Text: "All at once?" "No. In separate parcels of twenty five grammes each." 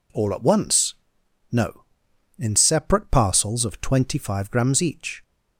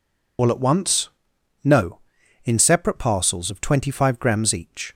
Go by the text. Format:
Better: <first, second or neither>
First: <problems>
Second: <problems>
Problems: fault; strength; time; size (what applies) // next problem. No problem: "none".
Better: first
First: none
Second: loses the start of "All"; at 0.3 s; 85 ms